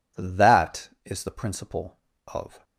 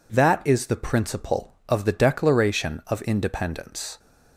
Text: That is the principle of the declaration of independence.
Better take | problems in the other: second | stops before "the declaration of independence"; at 2.6 s

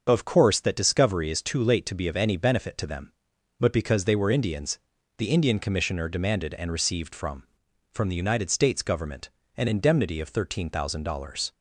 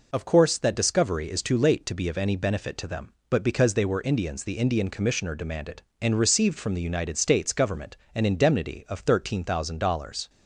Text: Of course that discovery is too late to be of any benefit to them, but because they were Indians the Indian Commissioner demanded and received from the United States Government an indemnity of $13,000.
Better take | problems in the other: second | starts louder than the rest; until 1.1 s; 6.5 dB // pauses between "Indians" and "the"; at 4.7 s; 0.40 s long // says "from" twice; at 7.9 s // pauses between "Government" and "an"; slight; at 9.2 s; 0.30 s long; slight in the second

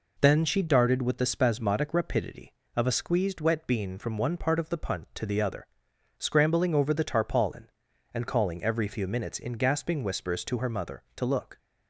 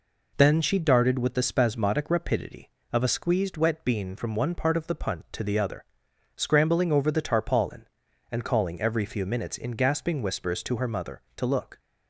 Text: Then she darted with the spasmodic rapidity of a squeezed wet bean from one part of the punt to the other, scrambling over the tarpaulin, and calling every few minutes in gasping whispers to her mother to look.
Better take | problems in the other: neither | none

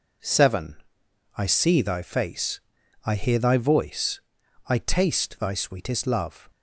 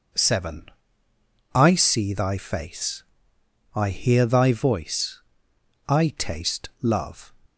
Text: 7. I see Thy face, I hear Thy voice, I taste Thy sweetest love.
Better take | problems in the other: first | skips "Thy sweetest"; at 6.7 s

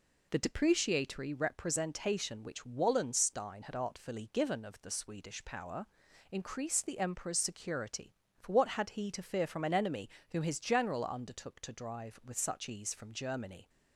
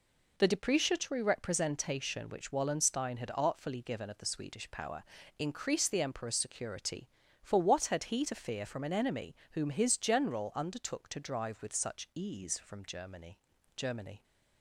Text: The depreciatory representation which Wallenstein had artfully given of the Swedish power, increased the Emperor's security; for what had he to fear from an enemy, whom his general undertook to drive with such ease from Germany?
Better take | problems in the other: first | says "Germany" twice; at 13.7 s

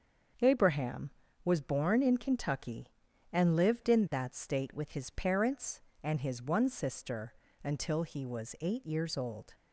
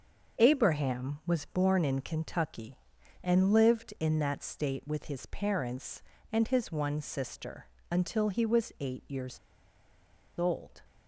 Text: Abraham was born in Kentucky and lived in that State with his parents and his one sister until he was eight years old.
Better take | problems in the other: first | starts louder than the rest; noticeable; until 1.4 s; 6 dB; also in the first // pauses between "sister" and "until"; slight; at 7.6 s; 0.22 s long; slight in the first // pauses between "years" and "old"; at 9.3 s; 0.99 s long

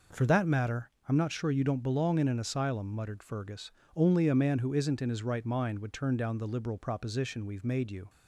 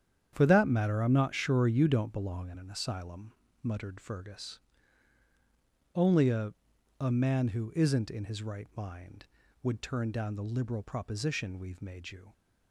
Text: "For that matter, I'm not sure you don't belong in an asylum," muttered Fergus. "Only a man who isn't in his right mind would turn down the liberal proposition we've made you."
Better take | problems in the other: first | starts louder than the rest; strong; until 1.3 s; 9 dB // says "a" twice; at 6.9 s

